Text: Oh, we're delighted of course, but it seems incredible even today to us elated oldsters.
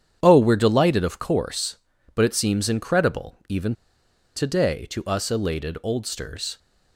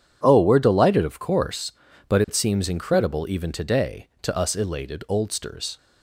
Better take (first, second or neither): second